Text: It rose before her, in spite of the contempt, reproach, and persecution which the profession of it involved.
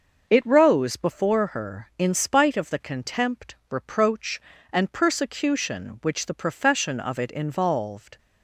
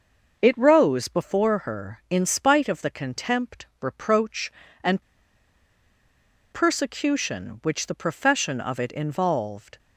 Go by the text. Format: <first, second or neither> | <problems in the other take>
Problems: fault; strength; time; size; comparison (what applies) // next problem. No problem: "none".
first | pauses between "and" and "persecution"; strong; at 5.0 s; 1.4 s long